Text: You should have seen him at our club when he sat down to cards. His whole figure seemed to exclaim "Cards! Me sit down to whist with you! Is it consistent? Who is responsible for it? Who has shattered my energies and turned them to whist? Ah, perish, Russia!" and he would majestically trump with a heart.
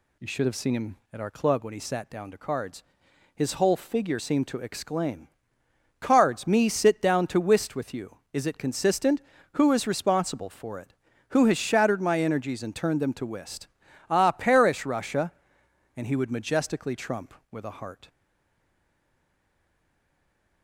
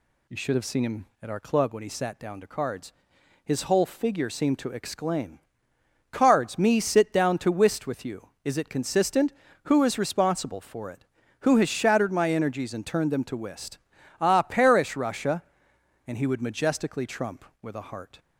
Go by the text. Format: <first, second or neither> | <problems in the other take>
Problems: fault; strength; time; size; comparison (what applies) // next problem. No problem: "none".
second | pauses between "exclaim" and "Cards"; noticeable; at 5.2 s; 0.72 s long; noticeable in the second // stays silent after the last word; strong; from 18.0 s on; 2.6 s long